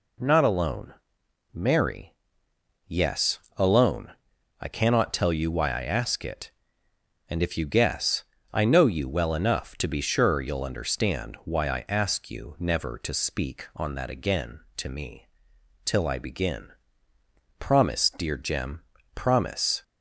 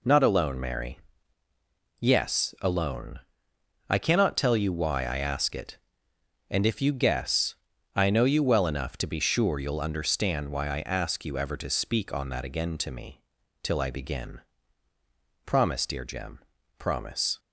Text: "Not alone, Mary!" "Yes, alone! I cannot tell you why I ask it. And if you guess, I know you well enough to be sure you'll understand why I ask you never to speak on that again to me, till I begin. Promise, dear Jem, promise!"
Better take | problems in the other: first | says "ever" for "never"; at 11.3 s

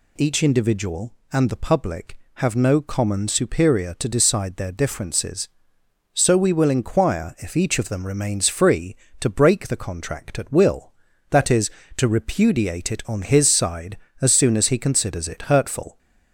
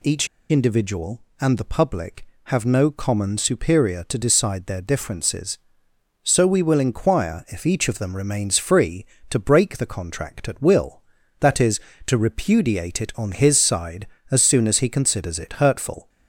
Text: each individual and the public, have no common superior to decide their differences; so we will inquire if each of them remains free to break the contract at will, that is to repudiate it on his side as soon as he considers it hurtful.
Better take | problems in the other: first | pauses between "each" and "individual"; slight; at 0.2 s; 0.23 s long

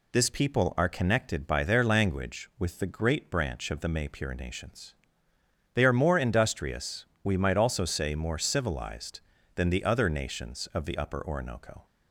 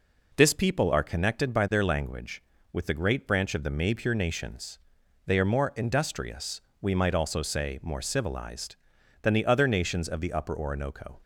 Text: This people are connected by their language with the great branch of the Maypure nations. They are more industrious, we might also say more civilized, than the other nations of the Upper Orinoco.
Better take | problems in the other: neither | none

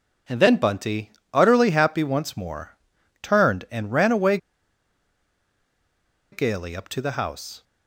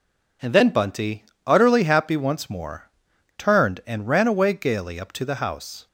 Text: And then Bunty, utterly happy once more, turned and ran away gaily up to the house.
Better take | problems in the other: second | pauses between "away" and "gaily"; strong; at 4.3 s; 1.9 s long

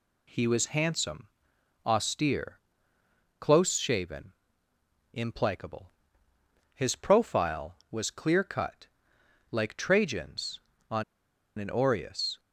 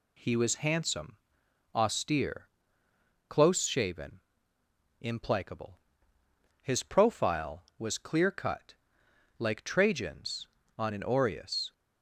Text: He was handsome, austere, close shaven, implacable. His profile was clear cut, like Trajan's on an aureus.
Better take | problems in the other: second | pauses between "on" and "an"; noticeable; at 11.0 s; 0.55 s long

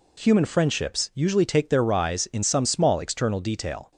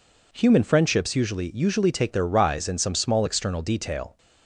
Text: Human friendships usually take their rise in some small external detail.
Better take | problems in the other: first | says "usually" twice; at 1.5 s

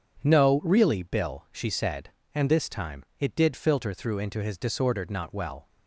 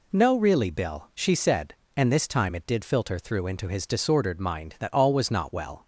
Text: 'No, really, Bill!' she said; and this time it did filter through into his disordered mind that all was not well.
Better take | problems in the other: second | pauses between "time" and "it"; slight; at 3.0 s; 0.16 s long // skips "mind that all was"; at 5.1 s

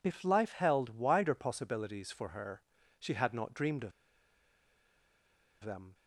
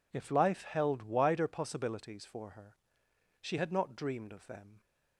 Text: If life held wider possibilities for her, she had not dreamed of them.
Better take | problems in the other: second | pauses between "of" and "them"; strong; at 3.9 s; 1.7 s long

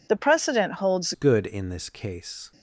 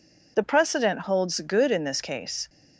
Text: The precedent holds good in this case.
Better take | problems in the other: second | changes voice at "good"; from 1.1 s on; 1.4 s long

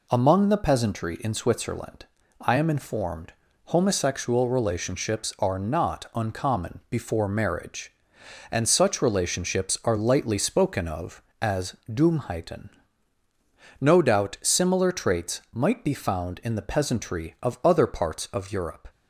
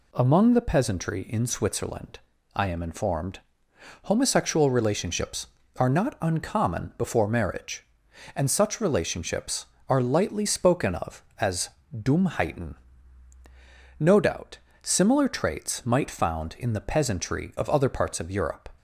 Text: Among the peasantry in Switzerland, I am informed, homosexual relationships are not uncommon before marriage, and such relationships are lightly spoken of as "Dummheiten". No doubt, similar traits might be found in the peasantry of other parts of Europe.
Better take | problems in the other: first | pauses between "as" and "Dummheiten"; slight; at 11.7 s; 0.22 s long // skips "be"; at 16.0 s

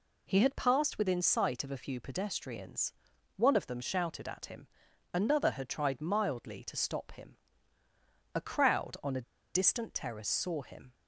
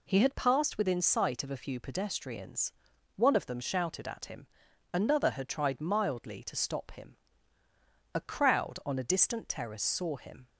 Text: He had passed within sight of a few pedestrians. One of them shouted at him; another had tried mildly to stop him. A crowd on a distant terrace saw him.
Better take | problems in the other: second | pauses between "a" and "distant"; slight; at 9.2 s; 0.31 s long

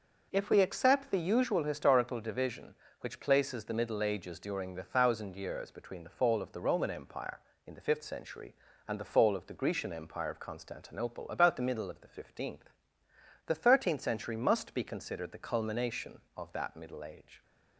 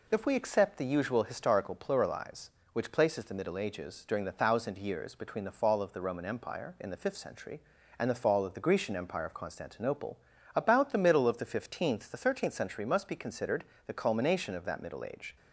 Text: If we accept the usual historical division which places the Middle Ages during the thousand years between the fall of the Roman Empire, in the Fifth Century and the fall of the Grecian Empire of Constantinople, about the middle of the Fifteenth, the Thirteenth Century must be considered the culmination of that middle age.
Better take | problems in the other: first | says "pluralize" for "division"; at 1.7 s // pauses between "considered" and "the"; slight; at 13.6 s; 0.20 s long

